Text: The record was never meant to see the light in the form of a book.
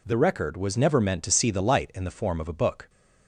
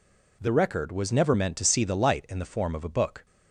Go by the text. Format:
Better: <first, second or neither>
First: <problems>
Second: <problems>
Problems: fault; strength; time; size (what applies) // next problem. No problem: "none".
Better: neither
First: none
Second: none